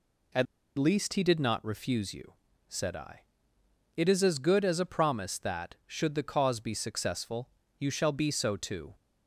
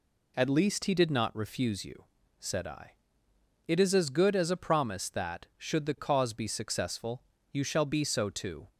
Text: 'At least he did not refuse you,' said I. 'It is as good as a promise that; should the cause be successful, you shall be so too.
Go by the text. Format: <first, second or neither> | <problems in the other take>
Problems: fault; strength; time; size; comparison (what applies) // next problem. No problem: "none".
second | pauses between "At" and "least"; slight; at 0.4 s; 0.33 s long